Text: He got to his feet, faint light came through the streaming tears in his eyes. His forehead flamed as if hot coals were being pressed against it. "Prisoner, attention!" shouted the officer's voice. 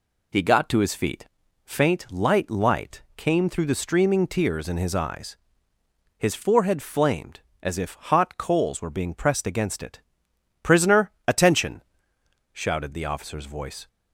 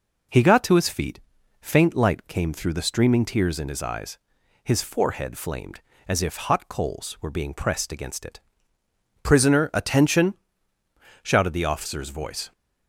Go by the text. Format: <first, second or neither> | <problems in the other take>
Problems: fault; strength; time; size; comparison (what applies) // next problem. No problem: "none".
second | says "light" twice; at 2.5 s